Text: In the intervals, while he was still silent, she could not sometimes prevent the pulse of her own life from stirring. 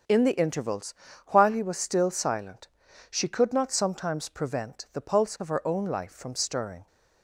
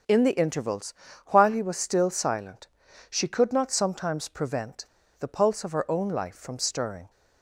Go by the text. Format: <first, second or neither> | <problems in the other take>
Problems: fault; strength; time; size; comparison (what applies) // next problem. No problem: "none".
first | starts louder than the rest; strong; until 1.4 s; 7.5 dB; also in the first // pauses between "prevent" and "the"; slight; at 4.8 s; 0.35 s long